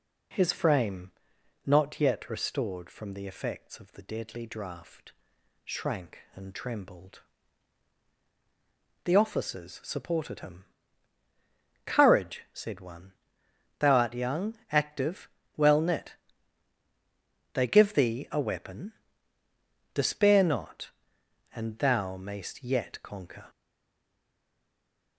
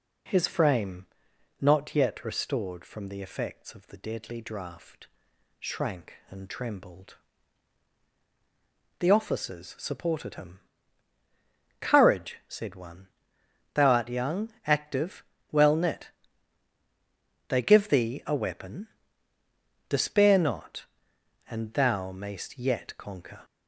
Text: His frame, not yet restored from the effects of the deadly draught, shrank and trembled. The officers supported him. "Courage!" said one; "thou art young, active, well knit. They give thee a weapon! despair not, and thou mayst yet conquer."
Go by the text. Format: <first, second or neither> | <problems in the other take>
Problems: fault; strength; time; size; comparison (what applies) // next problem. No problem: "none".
second | stays silent after the last word; noticeable; from 23.4 s on; 1.7 s long